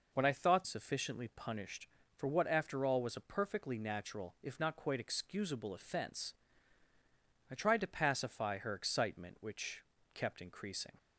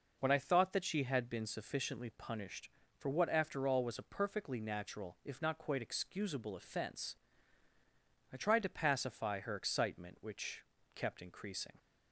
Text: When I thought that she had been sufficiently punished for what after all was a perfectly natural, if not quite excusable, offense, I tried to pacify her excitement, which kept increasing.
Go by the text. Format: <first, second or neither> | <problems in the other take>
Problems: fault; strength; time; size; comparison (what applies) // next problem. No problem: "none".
second | skips "that she had been"; at 0.6 s // pauses between "which" and "kept"; slight; at 9.8 s; 0.32 s long; slight in the second